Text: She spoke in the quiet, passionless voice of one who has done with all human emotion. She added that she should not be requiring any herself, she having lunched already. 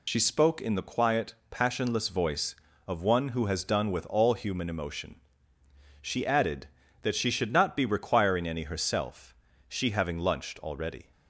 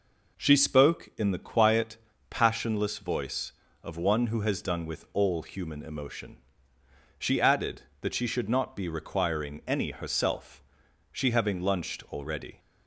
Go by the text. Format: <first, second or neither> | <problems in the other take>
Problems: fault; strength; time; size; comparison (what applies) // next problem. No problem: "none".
second | loses the start of "She"; at 0.0 s; 60 ms